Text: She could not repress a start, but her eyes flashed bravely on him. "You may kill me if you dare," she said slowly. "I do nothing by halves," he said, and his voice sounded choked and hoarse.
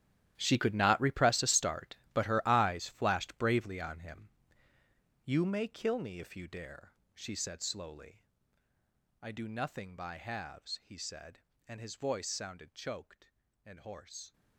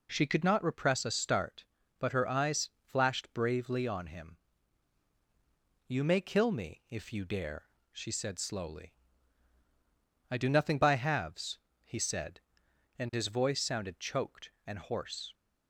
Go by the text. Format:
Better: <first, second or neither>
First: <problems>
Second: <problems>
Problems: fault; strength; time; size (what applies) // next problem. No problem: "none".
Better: second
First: gets quieter; strong; throughout; 16 dB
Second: none